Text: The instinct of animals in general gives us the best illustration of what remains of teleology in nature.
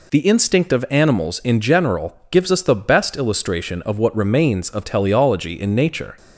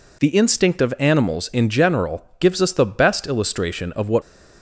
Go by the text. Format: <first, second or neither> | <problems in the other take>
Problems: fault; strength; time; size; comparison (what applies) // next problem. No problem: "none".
first | stops before "remains of teleology in nature"; at 4.2 s